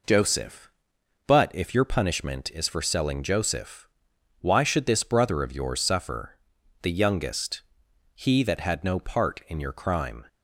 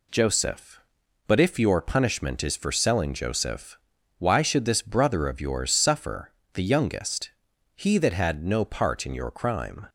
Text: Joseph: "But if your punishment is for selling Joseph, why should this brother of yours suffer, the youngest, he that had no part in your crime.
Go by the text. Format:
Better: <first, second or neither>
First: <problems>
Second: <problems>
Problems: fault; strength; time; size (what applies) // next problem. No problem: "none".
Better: neither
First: none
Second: none